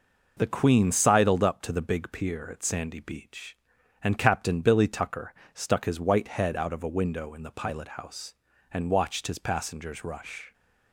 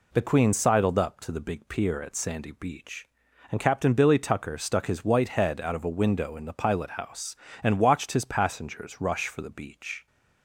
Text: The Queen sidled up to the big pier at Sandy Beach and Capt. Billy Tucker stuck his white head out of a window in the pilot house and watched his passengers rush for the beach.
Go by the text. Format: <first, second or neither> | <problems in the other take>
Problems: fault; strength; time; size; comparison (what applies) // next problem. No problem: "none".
second | pauses between "Tucker" and "stuck"; slight; at 5.3 s; 0.20 s long // stops before "for the beach"; at 10.5 s